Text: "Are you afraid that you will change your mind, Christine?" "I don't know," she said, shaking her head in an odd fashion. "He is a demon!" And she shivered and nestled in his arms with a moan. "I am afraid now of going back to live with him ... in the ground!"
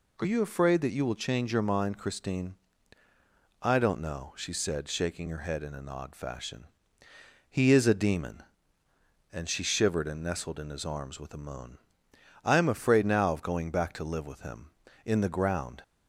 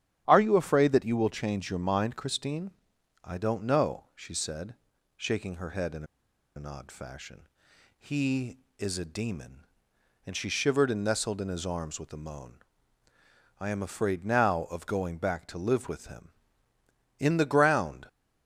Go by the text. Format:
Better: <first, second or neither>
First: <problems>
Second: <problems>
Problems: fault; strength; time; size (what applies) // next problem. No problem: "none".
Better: first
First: none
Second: starts louder than the rest; strong; until 1.2 s; 10.5 dB // pauses between "in" and "an"; noticeable; at 6.0 s; 0.51 s long